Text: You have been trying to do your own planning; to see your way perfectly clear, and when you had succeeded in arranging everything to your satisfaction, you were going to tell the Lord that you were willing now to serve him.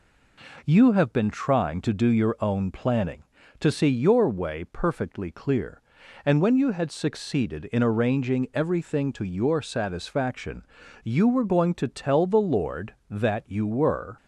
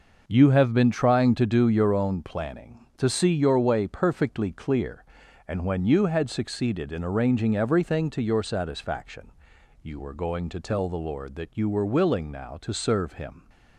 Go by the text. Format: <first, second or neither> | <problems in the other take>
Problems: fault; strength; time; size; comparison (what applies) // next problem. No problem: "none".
second | stops before "willing now to serve him"; at 14.1 s